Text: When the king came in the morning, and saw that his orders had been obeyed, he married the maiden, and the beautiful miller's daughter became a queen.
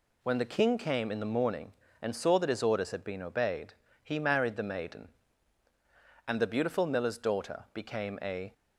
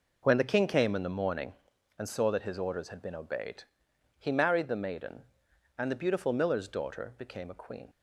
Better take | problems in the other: second | stops before "queen"; at 8.5 s

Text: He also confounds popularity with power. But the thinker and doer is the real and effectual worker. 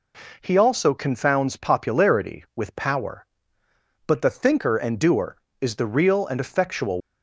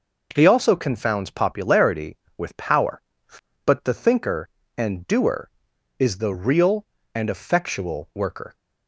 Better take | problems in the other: second | stops before "worker"; at 7.0 s

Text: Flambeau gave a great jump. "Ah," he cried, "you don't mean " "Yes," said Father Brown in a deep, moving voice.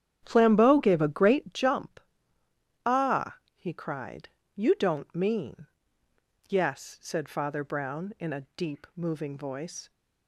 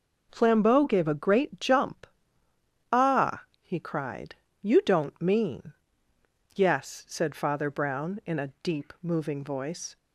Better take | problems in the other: second | starts louder than the rest; strong; until 1.6 s; 10 dB

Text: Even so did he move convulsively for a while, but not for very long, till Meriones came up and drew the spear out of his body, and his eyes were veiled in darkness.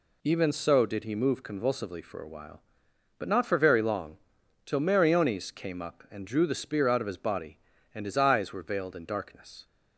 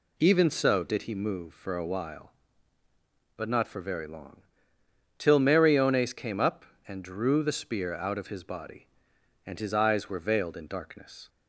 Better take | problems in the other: first | skips "convulsively"; at 1.5 s

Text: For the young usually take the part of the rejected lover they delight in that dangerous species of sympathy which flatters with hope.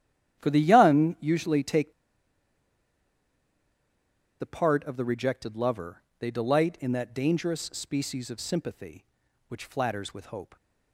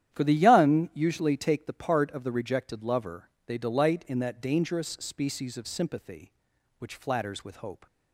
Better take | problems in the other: second | starts louder than the rest; strong; until 1.4 s; 11 dB; strong in the second // pauses between "take" and "the"; strong; at 1.9 s; 2.4 s long // pauses between "lover" and "they"; slight; at 6.0 s; 0.16 s long; slight in the second

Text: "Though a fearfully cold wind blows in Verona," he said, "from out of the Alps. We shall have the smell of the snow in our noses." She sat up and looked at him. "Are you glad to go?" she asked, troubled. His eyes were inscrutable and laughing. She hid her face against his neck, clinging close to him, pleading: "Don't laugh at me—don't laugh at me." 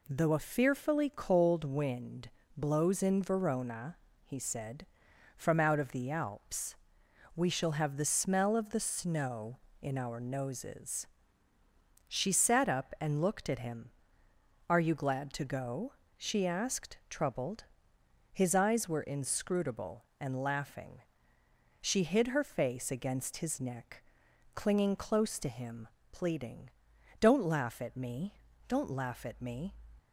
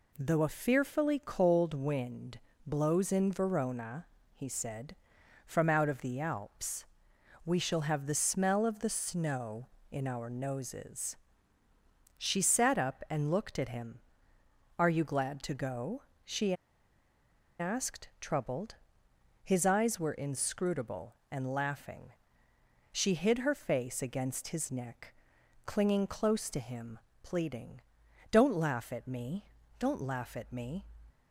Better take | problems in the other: first | pauses between "wind" and "blows"; slight; at 2.3 s; 0.28 s long; slight in the first // pauses between "she" and "asked"; at 16.5 s; 1.0 s long

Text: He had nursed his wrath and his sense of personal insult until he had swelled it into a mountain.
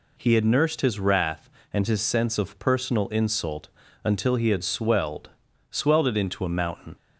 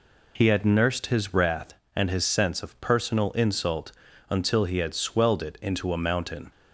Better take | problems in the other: second | pauses between "insult" and "until"; slight; at 3.6 s; 0.36 s long; slight in the second // says "swelled" twice; at 5.6 s

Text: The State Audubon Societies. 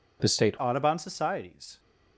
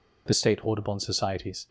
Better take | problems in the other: second | changes voice at "Audubon"; from 0.5 s on; 1.2 s long

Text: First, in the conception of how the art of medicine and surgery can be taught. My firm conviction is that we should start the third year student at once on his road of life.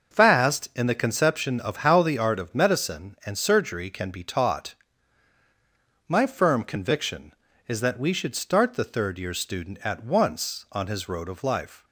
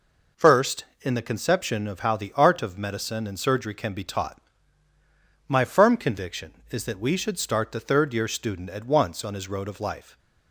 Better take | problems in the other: second | starts louder than the rest; until 1.2 s; 6 dB // says "Fast" for "First"; at 0.1 s

